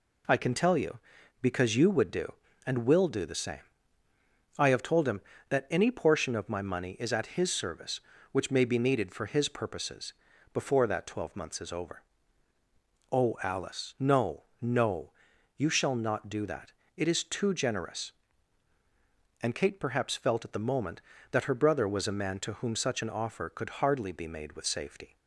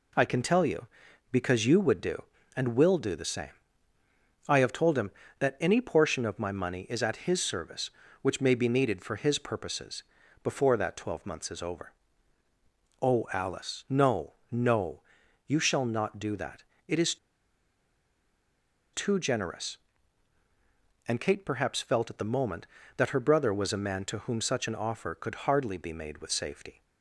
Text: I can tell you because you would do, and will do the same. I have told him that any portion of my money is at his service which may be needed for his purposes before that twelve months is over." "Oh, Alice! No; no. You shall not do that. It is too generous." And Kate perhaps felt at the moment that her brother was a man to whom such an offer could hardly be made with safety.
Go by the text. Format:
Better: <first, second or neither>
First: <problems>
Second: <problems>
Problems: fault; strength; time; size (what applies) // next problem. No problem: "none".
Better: first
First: pauses between "purposes" and "before"; at 10.1 s; 0.40 s long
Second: pauses between "purposes" and "before"; at 10.0 s; 0.40 s long // pauses between "is" and "too"; strong; at 17.1 s; 1.7 s long